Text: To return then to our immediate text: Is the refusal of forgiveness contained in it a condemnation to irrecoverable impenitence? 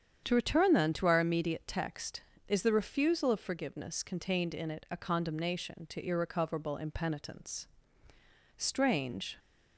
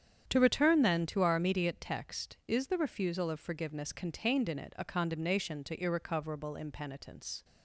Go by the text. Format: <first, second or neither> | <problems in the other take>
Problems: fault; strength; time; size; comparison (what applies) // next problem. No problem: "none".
second | starts louder than the rest; strong; until 1.2 s; 8 dB; strong in the second // goes on to say "Strange"; noticeable; from 8.5 s on; 0.80 s long